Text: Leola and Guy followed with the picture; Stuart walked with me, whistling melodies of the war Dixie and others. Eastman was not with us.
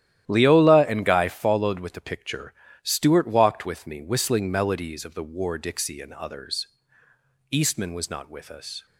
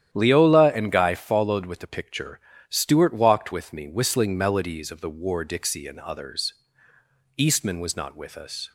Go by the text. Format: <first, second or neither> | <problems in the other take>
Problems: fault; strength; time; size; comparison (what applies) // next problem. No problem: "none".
second | gets quieter; strong; throughout; 12 dB // starts louder than the rest; strong; until 1.3 s; 12 dB; strong in the second